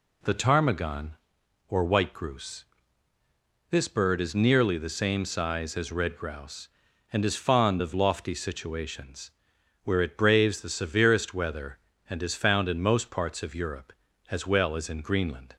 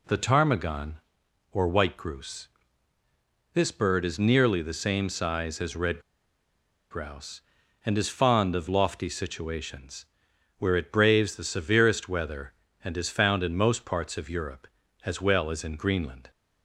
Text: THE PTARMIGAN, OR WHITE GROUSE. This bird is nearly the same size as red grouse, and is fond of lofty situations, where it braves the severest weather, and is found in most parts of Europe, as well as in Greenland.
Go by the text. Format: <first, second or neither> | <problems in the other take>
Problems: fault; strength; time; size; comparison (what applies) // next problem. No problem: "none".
first | pauses between "red" and "grouse"; noticeable; at 5.9 s; 0.91 s long